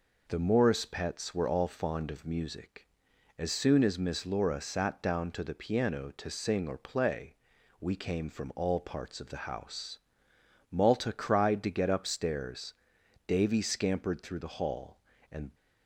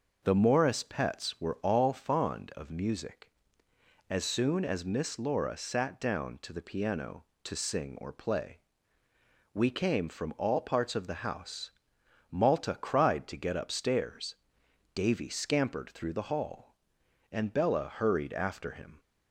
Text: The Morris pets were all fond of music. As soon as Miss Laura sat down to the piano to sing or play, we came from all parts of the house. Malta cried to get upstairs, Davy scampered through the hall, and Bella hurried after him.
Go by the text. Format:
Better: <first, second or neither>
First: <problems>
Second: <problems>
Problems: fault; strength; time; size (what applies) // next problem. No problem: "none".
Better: second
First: stops before "Bella hurried after him"; at 15.5 s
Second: none